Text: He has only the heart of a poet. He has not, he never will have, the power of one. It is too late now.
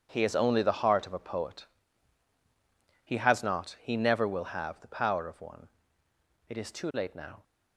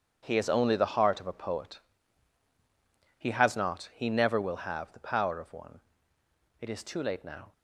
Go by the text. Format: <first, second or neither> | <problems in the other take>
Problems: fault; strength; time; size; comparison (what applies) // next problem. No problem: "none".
neither | starts louder than the rest; strong; the same in both